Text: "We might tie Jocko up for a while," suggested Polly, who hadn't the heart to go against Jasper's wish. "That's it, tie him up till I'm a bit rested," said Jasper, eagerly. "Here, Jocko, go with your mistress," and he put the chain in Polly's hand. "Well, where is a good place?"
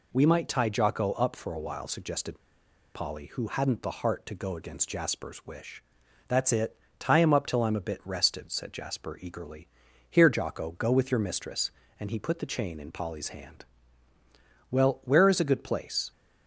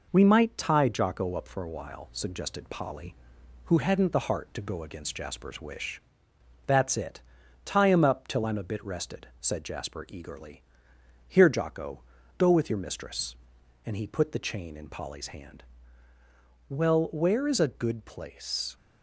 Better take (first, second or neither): second